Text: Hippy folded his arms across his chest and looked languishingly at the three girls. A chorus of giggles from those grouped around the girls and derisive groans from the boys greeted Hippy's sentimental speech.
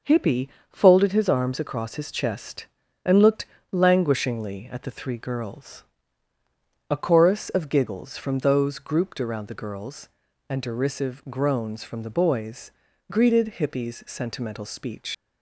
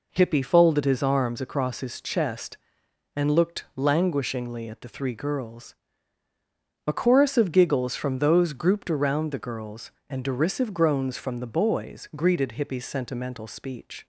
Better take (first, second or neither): second